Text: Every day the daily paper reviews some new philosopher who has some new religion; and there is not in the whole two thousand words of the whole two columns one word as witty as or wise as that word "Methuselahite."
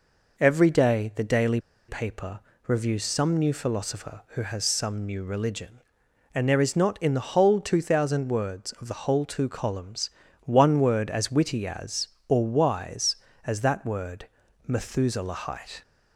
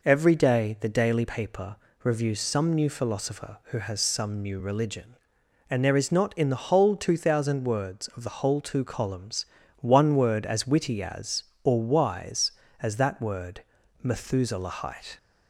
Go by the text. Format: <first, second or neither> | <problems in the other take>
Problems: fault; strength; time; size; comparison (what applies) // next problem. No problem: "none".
second | pauses between "daily" and "paper"; slight; at 1.6 s; 0.27 s long // pauses between "paper" and "reviews"; slight; at 2.3 s; 0.28 s long; slight in the second // pauses between "columns" and "one"; slight; at 10.0 s; 0.36 s long; slight in the second // pauses between "word" and "Methuselahite"; at 14.2 s; 0.40 s long; also in the second